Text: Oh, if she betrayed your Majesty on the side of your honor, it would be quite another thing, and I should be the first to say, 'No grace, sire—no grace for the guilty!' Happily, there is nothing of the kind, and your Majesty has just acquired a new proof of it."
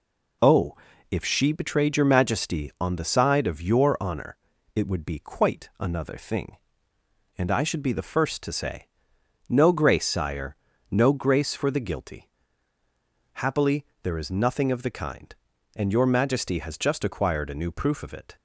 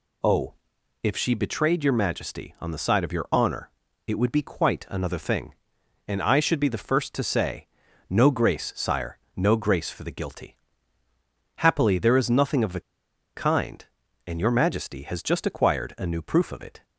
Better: first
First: none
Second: pauses between "the" and "kind"; noticeable; at 12.7 s; 0.55 s long

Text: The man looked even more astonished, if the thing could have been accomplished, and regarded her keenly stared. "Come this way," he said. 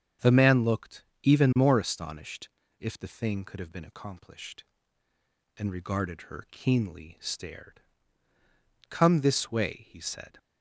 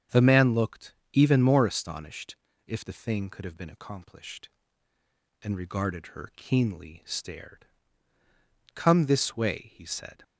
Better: neither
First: starts louder than the rest; strong; until 1.3 s; 7.5 dB // pauses between "looked" and "even"; slight; at 1.0 s; 0.18 s long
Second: starts louder than the rest; strong; until 1.2 s; 7.5 dB // pauses between "looked" and "even"; slight; at 0.9 s; 0.18 s long

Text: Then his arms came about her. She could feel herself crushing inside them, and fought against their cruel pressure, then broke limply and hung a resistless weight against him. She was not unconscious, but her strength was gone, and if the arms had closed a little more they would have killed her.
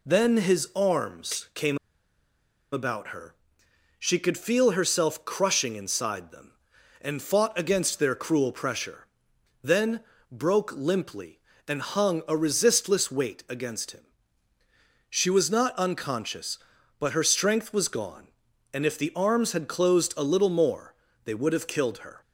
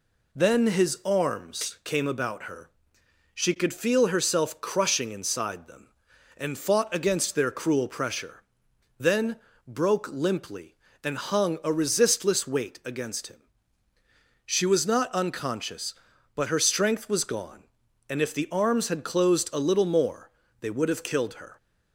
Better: second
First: pauses between "came" and "about"; noticeable; at 1.7 s; 0.94 s long // pauses between "then" and "broke"; slight; at 10.0 s; 0.30 s long // pauses between "more" and "they"; slight; at 20.9 s; 0.30 s long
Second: pauses between "then" and "broke"; slight; at 9.3 s; 0.30 s long // pauses between "more" and "they"; slight; at 20.3 s; 0.30 s long

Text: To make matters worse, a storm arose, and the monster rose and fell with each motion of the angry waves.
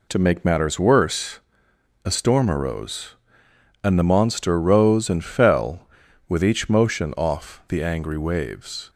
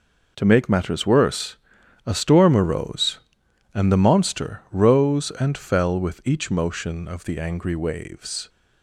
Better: second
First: says "off" for "of"; at 7.1 s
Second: none

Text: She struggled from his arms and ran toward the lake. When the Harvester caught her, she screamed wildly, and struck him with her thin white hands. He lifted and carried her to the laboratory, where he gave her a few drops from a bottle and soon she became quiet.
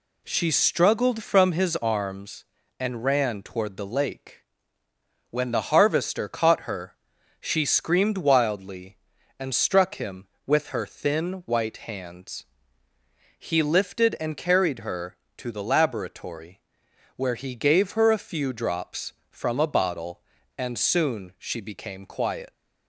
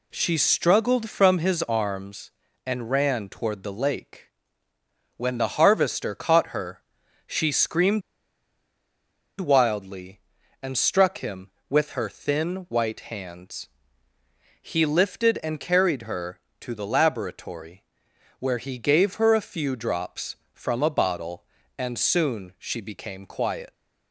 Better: first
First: none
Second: pauses between "screamed" and "wildly"; strong; at 8.0 s; 1.3 s long

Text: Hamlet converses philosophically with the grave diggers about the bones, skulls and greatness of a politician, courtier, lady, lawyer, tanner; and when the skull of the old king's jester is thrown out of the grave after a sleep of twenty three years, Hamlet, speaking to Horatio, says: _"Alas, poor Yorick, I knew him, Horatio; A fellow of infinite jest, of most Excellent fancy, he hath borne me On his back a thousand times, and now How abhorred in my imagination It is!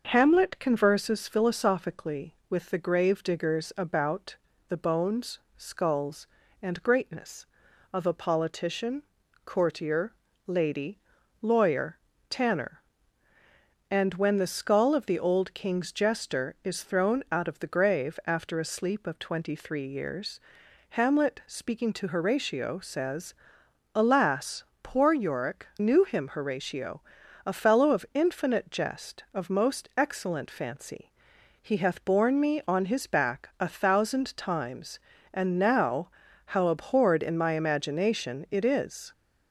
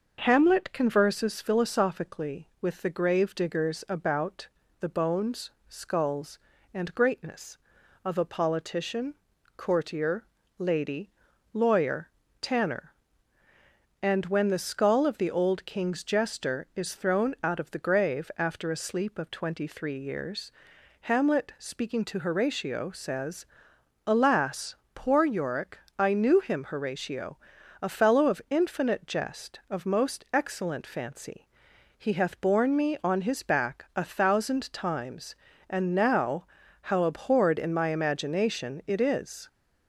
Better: second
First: starts louder than the rest; noticeable; until 1.1 s; 6 dB // pauses between "about" and "the"; slight; at 4.3 s; 0.32 s long // skips "I"; at 25.7 s // pauses between "now" and "How"; slight; at 36.0 s; 0.36 s long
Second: starts louder than the rest; noticeable; until 1.2 s; 6 dB // pauses between "about" and "the"; slight; at 4.4 s; 0.32 s long // pauses between "now" and "How"; slight; at 36.4 s; 0.36 s long

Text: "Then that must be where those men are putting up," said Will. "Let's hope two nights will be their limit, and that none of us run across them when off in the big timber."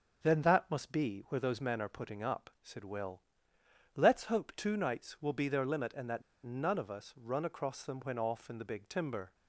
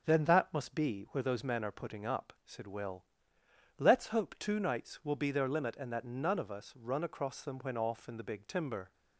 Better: second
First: starts louder than the rest; until 1.3 s; 7 dB // pauses between "that" and "none"; slight; at 6.2 s; 0.23 s long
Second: starts louder than the rest; until 1.1 s; 7 dB

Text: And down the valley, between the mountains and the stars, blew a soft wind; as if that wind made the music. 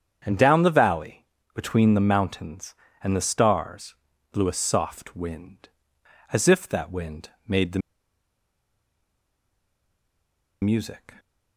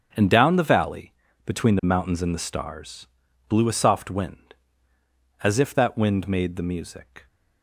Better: second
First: starts louder than the rest; strong; until 1.2 s; 8 dB // pauses between "the" and "music"; strong; at 7.8 s; 2.8 s long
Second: starts louder than the rest; strong; until 1.4 s; 7.5 dB

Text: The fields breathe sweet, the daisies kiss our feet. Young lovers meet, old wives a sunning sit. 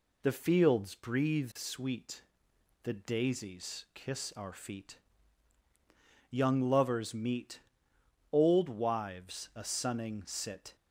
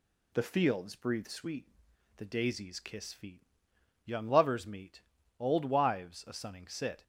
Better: first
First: none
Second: skips "our"; at 3.1 s

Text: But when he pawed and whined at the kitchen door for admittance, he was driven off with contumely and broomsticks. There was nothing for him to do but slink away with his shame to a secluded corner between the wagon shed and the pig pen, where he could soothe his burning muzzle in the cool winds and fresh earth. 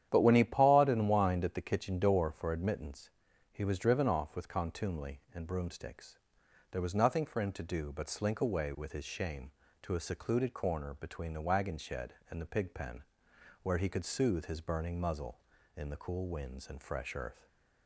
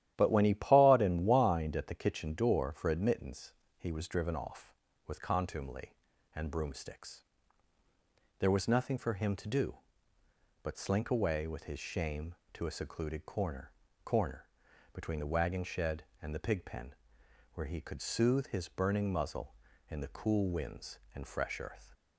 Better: first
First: starts louder than the rest; strong; until 1.1 s; 10 dB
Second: starts louder than the rest; strong; until 1.1 s; 12 dB // says "corner" twice; at 14.0 s

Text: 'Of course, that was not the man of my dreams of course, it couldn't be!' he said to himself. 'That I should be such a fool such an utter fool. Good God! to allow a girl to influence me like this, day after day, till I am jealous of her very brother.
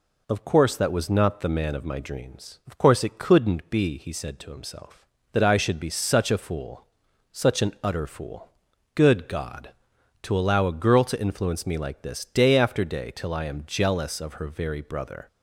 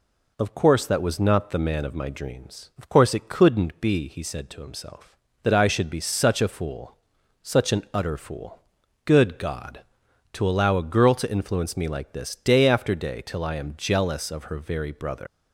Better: first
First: pauses between "fool" and "such"; noticeable; at 6.8 s; 0.48 s long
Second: pauses between "fool" and "such"; noticeable; at 6.9 s; 0.48 s long // leaves "brother" unfinished; at 15.2 s; 110 ms

